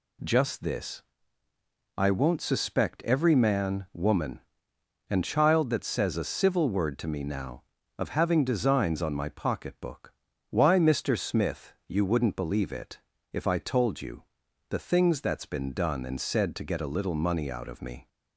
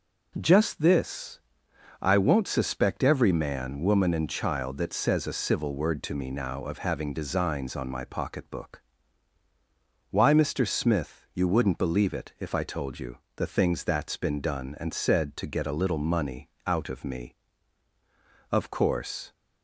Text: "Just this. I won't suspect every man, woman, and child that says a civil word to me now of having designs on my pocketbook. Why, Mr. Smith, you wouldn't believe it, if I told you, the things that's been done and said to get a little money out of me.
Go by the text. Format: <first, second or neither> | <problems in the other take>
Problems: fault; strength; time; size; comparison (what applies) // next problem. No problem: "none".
first | pauses between "money" and "out"; slight; at 16.4 s; 0.18 s long // goes on to say "Of course"; noticeable; from 18.4 s on; 0.82 s long